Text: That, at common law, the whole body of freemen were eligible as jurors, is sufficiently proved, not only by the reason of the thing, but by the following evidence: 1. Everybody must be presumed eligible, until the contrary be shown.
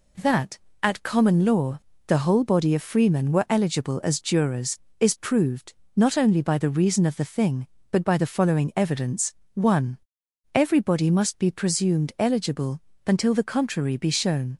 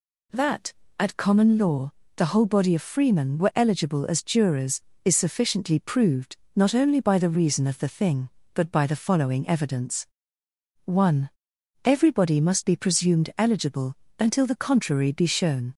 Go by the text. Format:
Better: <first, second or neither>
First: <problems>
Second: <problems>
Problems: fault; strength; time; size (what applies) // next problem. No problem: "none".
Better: second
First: skips "sufficiently"; at 5.1 s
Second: none